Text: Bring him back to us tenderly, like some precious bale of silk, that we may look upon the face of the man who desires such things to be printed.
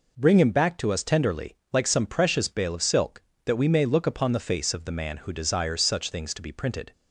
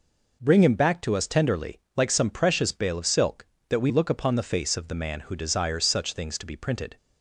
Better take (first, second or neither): first